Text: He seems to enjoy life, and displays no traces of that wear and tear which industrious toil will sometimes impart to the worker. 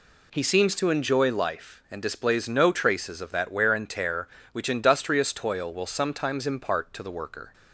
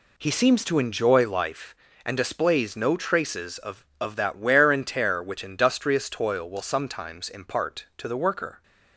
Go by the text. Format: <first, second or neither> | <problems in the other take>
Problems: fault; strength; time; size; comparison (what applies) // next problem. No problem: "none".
first | says "of" twice; at 4.0 s